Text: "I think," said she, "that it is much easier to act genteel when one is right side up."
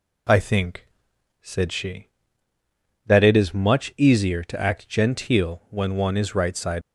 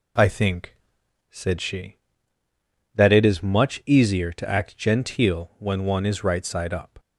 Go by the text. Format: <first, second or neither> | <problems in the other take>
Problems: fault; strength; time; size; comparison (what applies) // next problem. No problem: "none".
second | stops before "up"; at 6.8 s